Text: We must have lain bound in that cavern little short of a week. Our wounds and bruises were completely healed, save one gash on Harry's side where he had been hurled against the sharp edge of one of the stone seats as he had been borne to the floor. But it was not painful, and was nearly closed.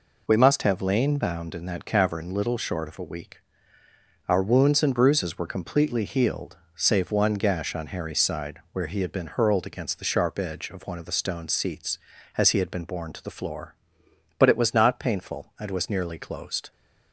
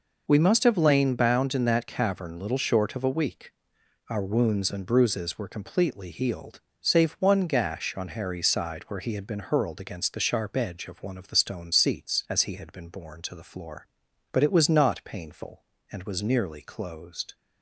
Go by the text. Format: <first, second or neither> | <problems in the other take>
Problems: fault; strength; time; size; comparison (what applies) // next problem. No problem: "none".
neither | none